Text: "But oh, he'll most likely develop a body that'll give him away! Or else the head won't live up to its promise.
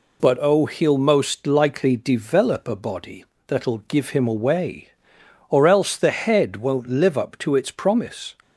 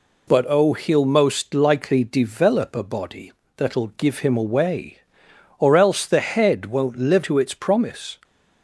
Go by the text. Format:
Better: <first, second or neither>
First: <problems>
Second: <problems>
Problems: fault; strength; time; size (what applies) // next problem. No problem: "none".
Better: first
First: pauses between "body" and "that'll"; slight; at 3.2 s; 0.22 s long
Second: pauses between "body" and "that'll"; slight; at 3.3 s; 0.24 s long // skips "up"; at 7.2 s